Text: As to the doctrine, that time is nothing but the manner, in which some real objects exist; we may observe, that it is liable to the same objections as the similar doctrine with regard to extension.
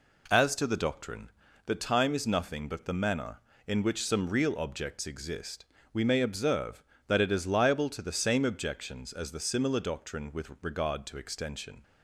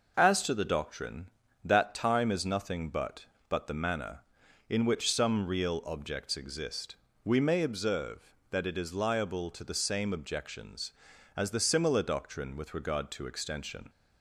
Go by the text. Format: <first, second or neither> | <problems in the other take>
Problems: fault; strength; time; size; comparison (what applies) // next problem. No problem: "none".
first | says "but" twice; at 3.4 s